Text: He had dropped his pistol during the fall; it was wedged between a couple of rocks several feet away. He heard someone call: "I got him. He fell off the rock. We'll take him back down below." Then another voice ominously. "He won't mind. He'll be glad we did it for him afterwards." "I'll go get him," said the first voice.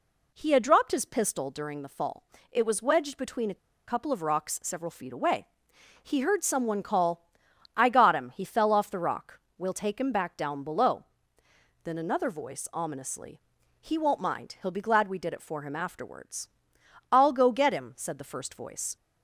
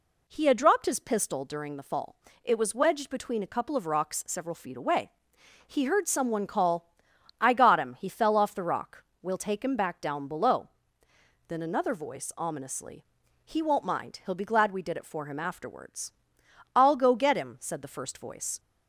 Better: second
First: pauses between "a" and "couple"; slight; at 3.5 s; 0.30 s long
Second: none

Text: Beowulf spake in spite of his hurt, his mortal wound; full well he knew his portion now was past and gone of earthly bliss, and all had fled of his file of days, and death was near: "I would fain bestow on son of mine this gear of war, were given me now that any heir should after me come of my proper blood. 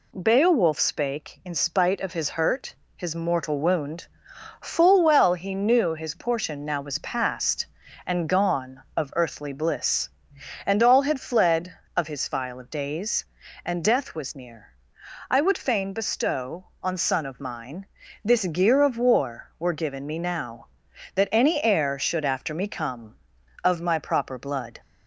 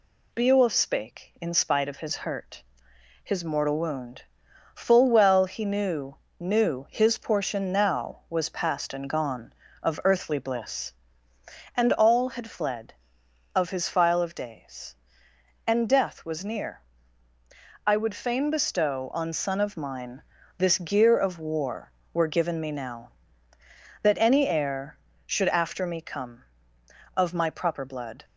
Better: first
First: pauses between "mine" and "this"; at 17.8 s; 0.40 s long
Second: says "knew" twice; at 6.4 s // pauses between "mine" and "this"; slight; at 20.2 s; 0.34 s long

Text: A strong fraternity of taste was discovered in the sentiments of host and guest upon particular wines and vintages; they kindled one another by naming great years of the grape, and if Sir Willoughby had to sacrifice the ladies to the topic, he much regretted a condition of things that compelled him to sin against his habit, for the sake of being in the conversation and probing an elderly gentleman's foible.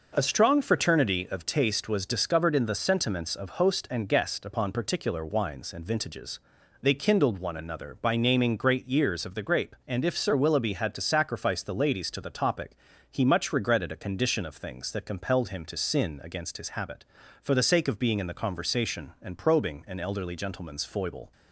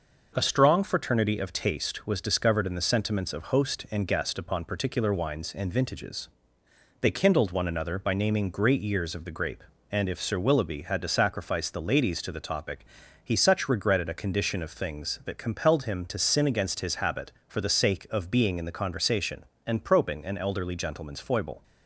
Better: first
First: none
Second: says "such" for "much"; at 13.3 s

